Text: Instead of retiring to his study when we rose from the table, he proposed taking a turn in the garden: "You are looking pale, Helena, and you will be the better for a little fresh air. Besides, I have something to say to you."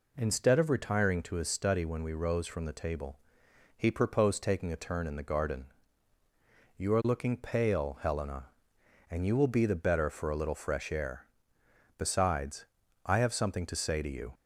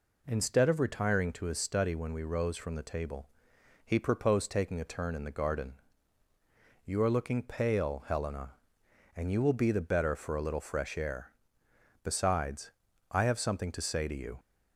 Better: neither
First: none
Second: none

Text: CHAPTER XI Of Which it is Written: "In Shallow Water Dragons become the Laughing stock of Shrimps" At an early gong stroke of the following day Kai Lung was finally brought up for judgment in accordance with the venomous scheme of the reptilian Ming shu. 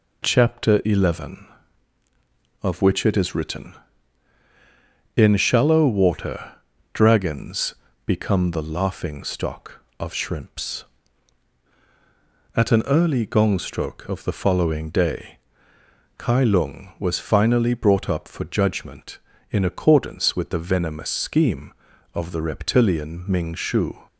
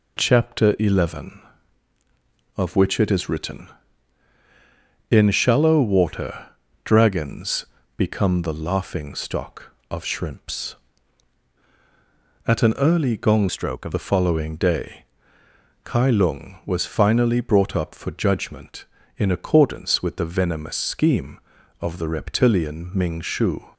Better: first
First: pauses between "Water" and "Dragons"; at 6.5 s; 0.39 s long // pauses between "Dragons" and "become"; slight; at 7.7 s; 0.30 s long // pauses between "day" and "Kai"; noticeable; at 15.3 s; 0.80 s long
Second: pauses between "Water" and "Dragons"; slight; at 6.4 s; 0.36 s long // pauses between "Dragons" and "become"; slight; at 7.6 s; 0.30 s long // changes voice from "stroke" to "of"; from 13.4 to 13.9 s; 0.5 s long // pauses between "day" and "Kai"; noticeable; at 15.0 s; 0.80 s long

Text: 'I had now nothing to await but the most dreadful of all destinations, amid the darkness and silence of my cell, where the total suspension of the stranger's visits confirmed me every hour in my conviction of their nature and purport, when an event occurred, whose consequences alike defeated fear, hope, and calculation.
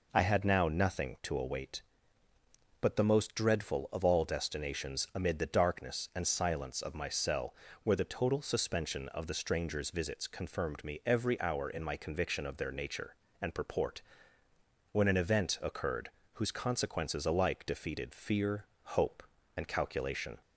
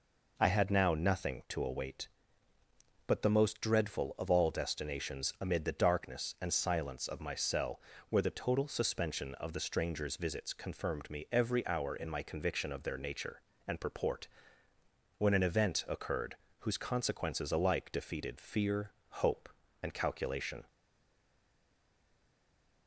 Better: first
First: none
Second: stays silent after the last word; from 20.6 s on; 2.2 s long

